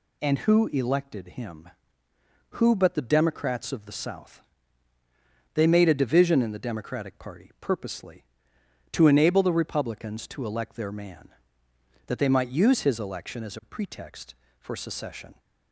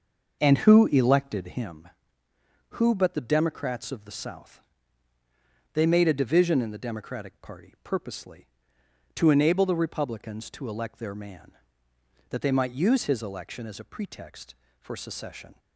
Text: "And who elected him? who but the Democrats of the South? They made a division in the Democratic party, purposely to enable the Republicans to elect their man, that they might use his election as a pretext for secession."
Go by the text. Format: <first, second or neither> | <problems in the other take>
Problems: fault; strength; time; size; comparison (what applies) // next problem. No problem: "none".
first | starts louder than the rest; noticeable; until 1.8 s; 6 dB